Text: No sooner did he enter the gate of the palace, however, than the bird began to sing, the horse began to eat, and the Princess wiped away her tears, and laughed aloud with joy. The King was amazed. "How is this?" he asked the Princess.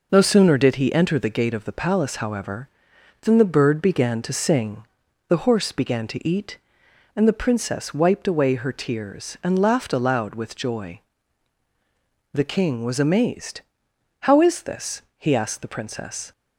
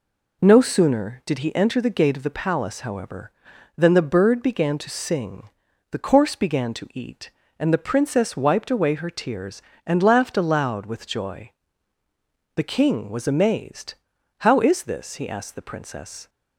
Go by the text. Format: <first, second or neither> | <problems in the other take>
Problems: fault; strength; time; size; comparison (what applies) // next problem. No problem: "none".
first | says "course" for "horse"; at 5.9 s